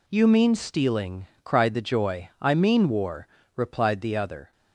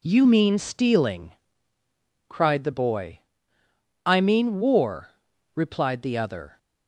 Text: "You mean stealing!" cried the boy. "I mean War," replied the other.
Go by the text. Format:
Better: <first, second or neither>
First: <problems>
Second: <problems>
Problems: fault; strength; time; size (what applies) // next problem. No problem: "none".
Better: second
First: says "joy" for "boy"; at 1.8 s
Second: none